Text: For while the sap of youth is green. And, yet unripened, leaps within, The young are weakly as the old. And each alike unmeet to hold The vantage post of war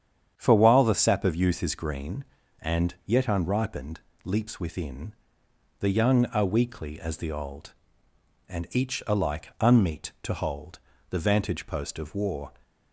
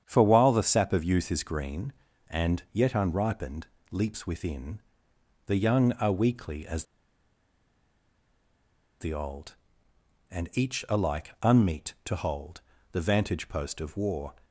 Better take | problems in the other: first | starts louder than the rest; strong; until 1.0 s; 8.5 dB; strong in the first // pauses between "as" and "the"; strong; at 6.8 s; 2.1 s long // pauses between "hold" and "The"; slight; at 12.6 s; 0.30 s long; slight in the first

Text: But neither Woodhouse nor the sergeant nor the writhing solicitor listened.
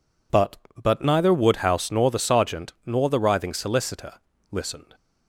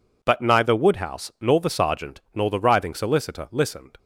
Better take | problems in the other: second | says "But" twice; at 0.8 s // pauses between "solicitor" and "listened"; at 4.1 s; 0.40 s long

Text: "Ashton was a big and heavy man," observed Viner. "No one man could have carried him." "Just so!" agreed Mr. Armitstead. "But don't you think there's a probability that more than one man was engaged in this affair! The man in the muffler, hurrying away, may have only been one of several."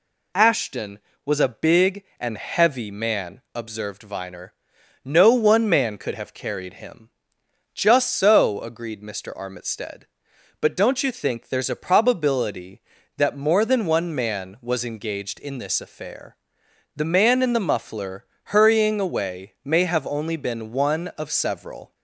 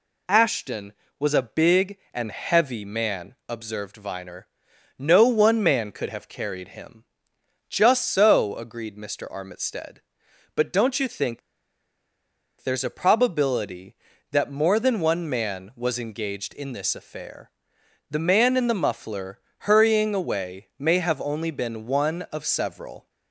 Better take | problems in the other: first | pauses between "think" and "there's"; at 11.4 s; 1.2 s long

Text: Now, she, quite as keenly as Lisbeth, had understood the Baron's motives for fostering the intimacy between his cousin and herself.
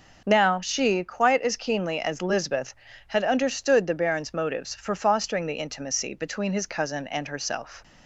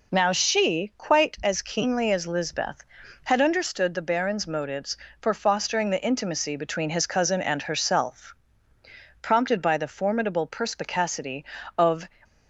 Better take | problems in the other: first | goes on to say "Prompted by the formidable perspicacity of"; strong; from 9.2 s on; 2.8 s long

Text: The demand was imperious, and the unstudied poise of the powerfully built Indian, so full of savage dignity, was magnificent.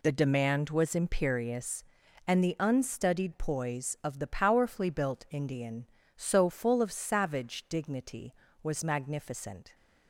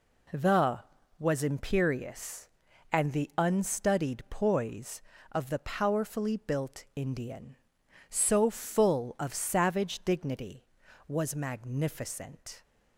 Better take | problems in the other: first | skips "demand"; at 0.9 s

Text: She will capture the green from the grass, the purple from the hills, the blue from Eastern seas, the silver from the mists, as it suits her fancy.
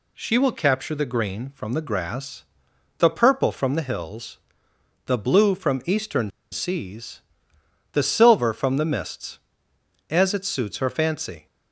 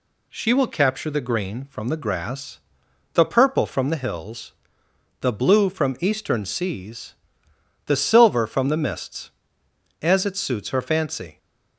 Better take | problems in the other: second | pauses between "Eastern" and "seas"; slight; at 6.3 s; 0.21 s long

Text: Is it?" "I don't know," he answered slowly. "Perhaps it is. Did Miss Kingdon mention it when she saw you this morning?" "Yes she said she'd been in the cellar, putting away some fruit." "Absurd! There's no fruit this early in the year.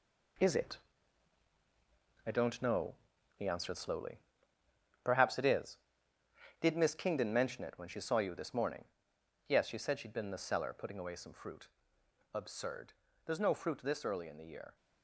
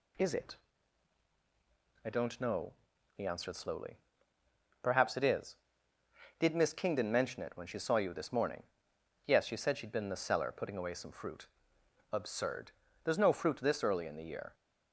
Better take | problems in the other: second | gets quieter; strong; throughout; 8 dB

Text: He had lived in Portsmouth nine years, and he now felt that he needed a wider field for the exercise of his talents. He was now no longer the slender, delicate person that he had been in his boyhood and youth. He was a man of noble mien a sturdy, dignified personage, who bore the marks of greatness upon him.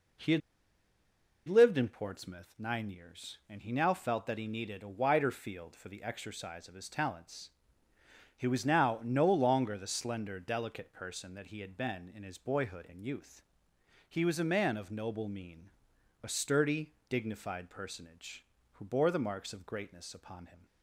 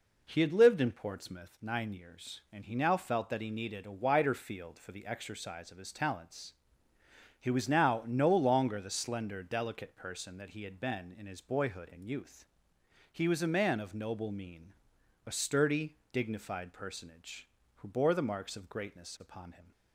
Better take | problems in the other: second | pauses between "had" and "lived"; at 0.4 s; 1.0 s long // pauses between "mien" and "a"; noticeable; at 15.7 s; 0.52 s long; noticeable in the second

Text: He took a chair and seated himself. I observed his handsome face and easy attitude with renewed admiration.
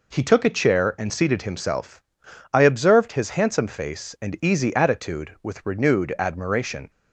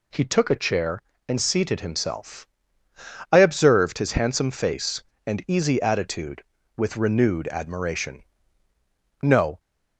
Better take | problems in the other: first | goes on to say "No"; slight; from 9.2 s on; 0.38 s long

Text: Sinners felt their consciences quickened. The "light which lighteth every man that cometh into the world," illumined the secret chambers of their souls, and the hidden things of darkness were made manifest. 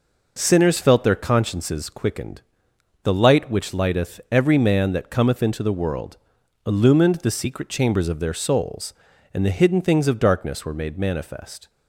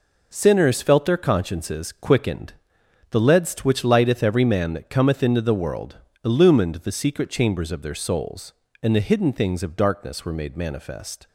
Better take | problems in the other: first | says "ledst" for "light"; at 3.1 s

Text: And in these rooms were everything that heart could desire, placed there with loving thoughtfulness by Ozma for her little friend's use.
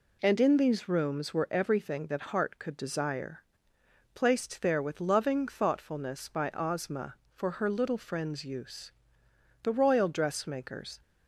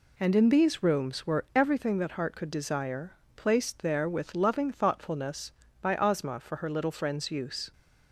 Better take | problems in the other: second | goes on to say "The royal dressmakers"; from 9.6 s on; 1.3 s long

